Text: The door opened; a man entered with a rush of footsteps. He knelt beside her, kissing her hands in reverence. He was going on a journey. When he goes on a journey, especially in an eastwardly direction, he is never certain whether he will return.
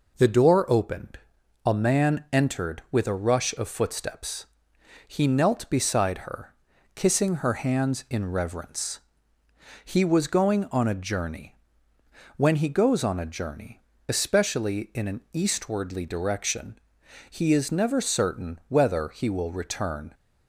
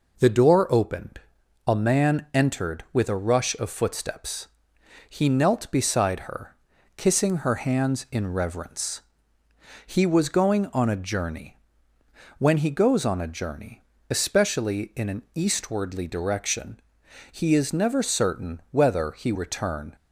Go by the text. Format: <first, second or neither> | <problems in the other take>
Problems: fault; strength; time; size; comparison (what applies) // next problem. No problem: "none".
first | skips "will"; at 19.3 s